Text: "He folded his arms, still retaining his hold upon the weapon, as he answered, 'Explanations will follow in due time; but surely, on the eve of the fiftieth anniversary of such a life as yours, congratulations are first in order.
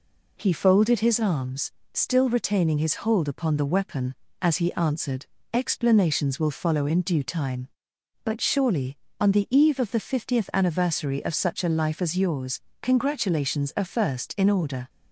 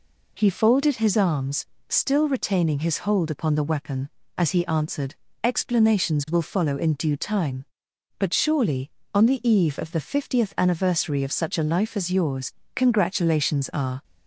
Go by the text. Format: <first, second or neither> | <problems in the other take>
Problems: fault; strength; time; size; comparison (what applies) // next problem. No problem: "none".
first | stops before "first in order"; at 14.0 s